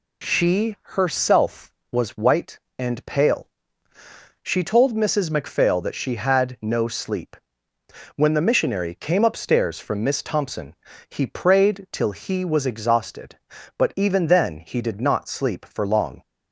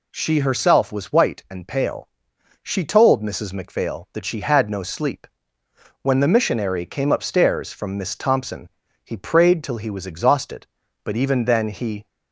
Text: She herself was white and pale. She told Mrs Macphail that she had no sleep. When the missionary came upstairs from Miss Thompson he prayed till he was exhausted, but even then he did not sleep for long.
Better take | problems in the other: first | pauses between "Thompson" and "he"; slight; at 8.7 s; 0.34 s long; slight in the first // stops before "did not sleep for long"; at 12.0 s

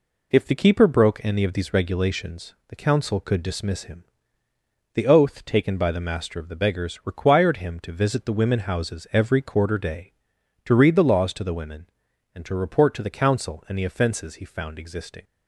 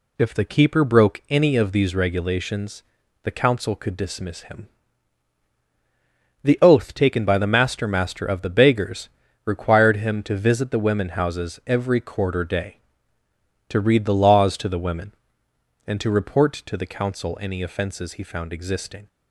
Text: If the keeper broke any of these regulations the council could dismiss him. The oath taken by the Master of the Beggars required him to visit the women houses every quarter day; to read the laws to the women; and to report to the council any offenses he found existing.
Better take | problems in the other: first | pauses between "regulations" and "the"; at 2.8 s; 0.40 s long; slight in the first // says "Master" twice; at 7.8 s // pauses between "Beggars" and "required"; slight; at 9.0 s; 0.36 s long

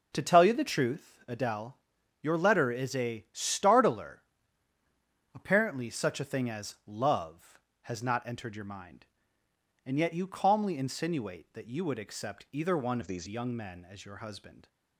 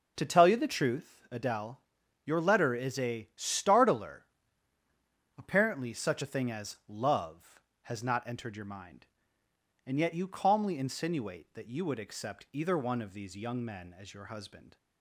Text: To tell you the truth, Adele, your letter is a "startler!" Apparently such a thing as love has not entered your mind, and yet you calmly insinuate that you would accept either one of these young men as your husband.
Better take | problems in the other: second | changes voice from "of" to "these"; from 13.0 to 13.2 s; 0.2 s long

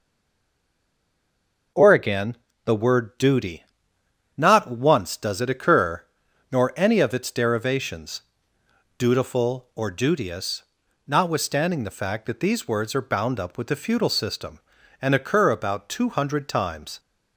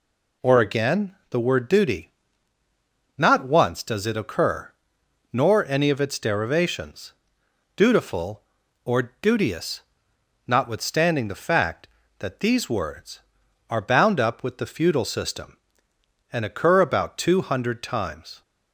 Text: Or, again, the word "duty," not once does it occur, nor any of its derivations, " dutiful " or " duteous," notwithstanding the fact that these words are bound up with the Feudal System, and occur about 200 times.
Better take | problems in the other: second | stays silent before the first word; noticeable; until 1.7 s; 1.7 s long // starts louder than the rest; noticeable; until 3.0 s; 6 dB

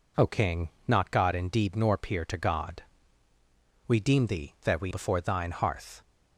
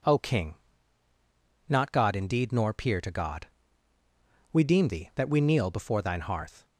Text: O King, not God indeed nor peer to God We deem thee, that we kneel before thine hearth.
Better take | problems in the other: second | pauses between "God" and "We"; at 2.8 s; 1.0 s long; also in the second // skips "kneel"; at 4.9 s

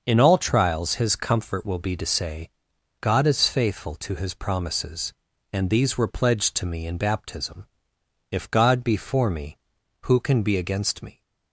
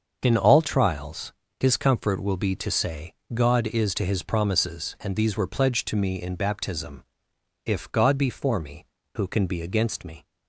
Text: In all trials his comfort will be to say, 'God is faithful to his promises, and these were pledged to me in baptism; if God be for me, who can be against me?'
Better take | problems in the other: first | starts louder than the rest; until 1.2 s; 6.5 dB; also in the first // pauses between "trials" and "his"; slight; at 1.3 s; 0.26 s long // skips "faithful"; at 3.9 s

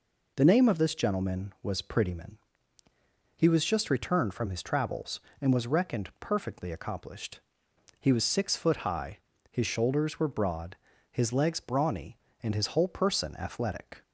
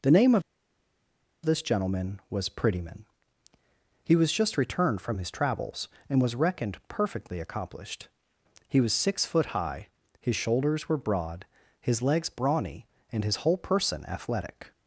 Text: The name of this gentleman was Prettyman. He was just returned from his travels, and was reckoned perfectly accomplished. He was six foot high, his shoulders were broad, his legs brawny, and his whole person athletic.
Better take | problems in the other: first | pauses between "of" and "this"; at 0.4 s; 1.0 s long

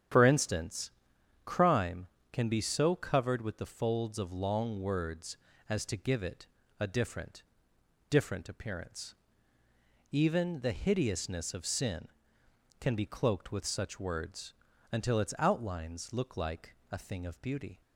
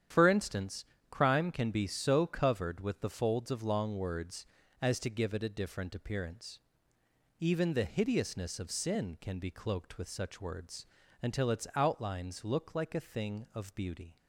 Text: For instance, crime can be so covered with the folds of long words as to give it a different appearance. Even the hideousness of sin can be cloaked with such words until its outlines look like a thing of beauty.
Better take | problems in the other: second | starts louder than the rest; strong; until 1.6 s; 9.5 dB; strong in the second // pauses between "it" and "a"; slight; at 6.4 s; 0.34 s long // says "different" twice; at 8.1 s // pauses between "words" and "until"; at 14.5 s; 0.38 s long; slight in the second // pauses between "like" and "a"; slight; at 16.7 s; 0.16 s long

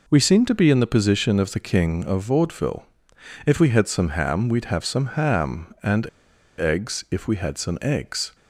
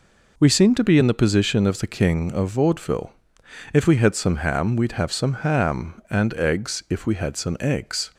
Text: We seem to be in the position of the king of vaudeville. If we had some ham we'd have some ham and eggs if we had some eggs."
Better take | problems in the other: second | pauses between "and" and "eggs"; noticeable; at 6.0 s; 0.51 s long

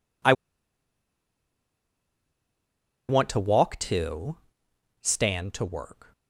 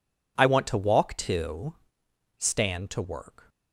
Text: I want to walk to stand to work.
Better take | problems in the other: second | pauses between "I" and "want"; strong; at 0.3 s; 2.7 s long // pauses between "to" and "stand"; noticeable; at 4.3 s; 0.64 s long; noticeable in the second

